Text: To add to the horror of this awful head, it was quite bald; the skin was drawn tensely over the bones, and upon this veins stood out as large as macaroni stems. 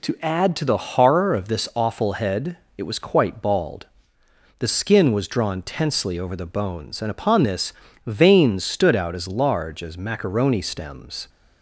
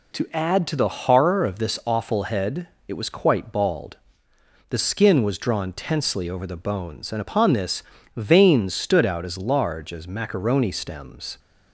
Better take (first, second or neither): neither